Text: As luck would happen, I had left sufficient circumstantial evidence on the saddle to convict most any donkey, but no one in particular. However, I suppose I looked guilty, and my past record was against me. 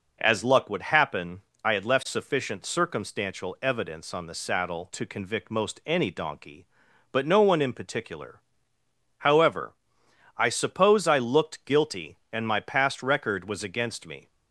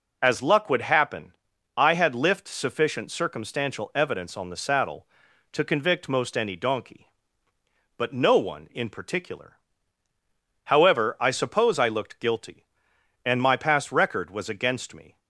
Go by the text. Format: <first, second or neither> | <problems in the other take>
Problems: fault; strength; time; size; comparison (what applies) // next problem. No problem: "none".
first | says "lift" for "left"; at 2.1 s